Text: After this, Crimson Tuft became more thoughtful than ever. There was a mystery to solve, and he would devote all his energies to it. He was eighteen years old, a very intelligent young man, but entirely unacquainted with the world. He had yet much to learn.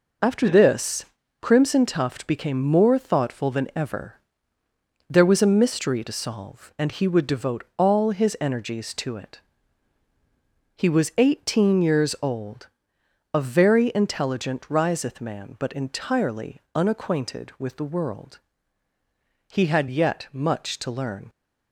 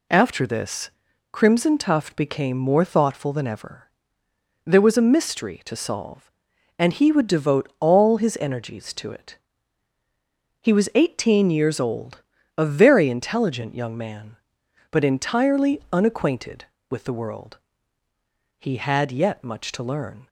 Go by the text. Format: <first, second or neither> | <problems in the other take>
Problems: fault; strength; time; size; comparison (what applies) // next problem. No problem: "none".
second | says "riseth" for "young"; at 14.6 s // pauses between "entirely" and "unacquainted"; slight; at 16.5 s; 0.18 s long